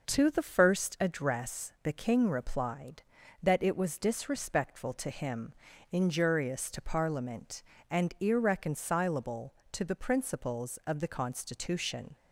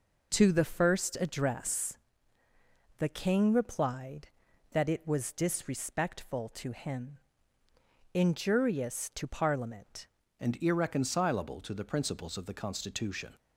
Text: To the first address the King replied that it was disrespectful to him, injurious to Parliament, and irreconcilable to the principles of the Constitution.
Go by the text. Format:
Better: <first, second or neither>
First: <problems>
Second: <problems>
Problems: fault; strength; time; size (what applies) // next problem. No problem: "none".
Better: first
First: none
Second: pauses between "address" and "the"; at 1.9 s; 1.0 s long // changes voice at "and"; from 10.4 s on; 2.9 s long